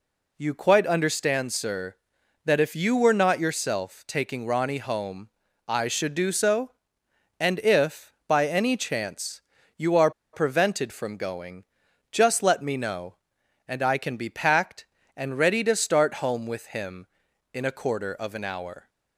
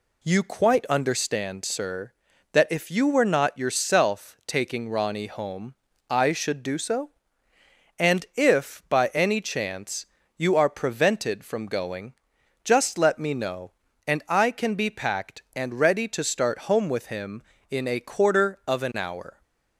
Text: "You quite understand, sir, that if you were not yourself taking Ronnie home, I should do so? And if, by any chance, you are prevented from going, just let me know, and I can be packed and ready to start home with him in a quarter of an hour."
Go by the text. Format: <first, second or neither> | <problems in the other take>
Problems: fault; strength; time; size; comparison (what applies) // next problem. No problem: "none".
second | pauses between "are" and "prevented"; slight; at 10.1 s; 0.22 s long